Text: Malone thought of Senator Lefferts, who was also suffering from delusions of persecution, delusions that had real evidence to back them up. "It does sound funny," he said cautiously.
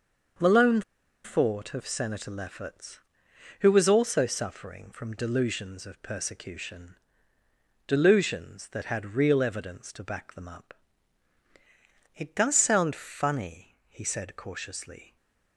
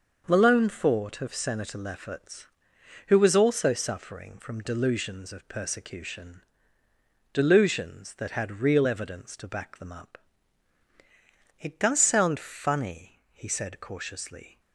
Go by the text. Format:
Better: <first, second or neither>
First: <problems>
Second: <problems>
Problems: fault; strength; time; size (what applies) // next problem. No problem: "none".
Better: second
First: starts louder than the rest; until 1.8 s; 6.5 dB // pauses between "Malone" and "thought"; at 0.8 s; 0.43 s long // stays silent after the last word; slight; from 15.0 s on; 0.5 s long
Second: starts louder than the rest; until 1.2 s; 6.5 dB